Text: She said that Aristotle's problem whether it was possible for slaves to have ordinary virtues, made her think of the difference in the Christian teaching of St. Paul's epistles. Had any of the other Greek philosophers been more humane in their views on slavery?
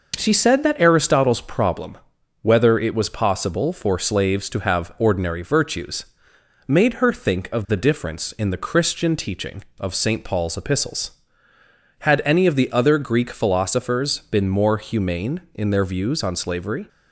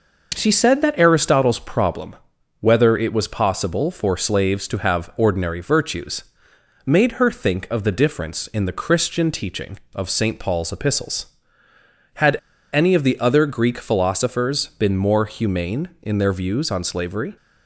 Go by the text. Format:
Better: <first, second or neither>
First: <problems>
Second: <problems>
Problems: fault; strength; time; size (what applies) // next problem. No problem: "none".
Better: first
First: pauses between "problem" and "whether"; noticeable; at 1.9 s; 0.46 s long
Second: pauses between "problem" and "whether"; noticeable; at 2.1 s; 0.46 s long // pauses between "Had" and "any"; slight; at 12.3 s; 0.35 s long